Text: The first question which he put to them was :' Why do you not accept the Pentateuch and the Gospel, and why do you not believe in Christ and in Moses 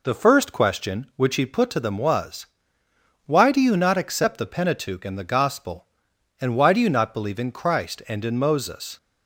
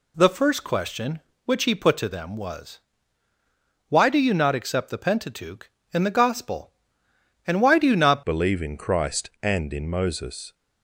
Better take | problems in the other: first | changes voice at "believe"; from 8.2 s on; 2.3 s long

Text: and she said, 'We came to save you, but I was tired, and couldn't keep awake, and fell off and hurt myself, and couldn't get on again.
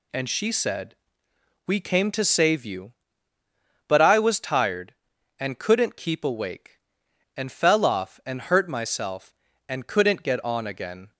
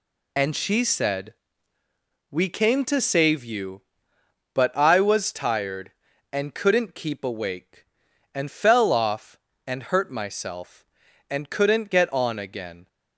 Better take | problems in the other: first | loses the start of "and"; at 0.3 s; 40 ms

